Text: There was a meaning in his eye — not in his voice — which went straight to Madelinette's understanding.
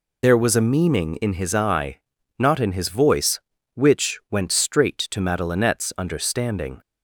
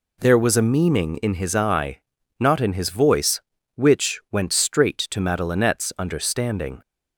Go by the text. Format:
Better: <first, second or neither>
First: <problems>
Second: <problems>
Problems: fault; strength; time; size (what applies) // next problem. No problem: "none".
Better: second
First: loses the start of "There"; at 0.2 s; 40 ms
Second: none